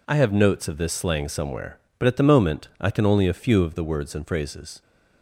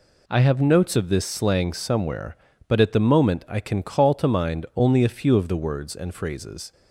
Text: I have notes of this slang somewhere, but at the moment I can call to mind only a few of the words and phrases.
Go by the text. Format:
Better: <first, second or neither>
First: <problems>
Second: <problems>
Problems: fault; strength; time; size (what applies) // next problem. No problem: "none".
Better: second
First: skips "call to mind"; at 3.0 s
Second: none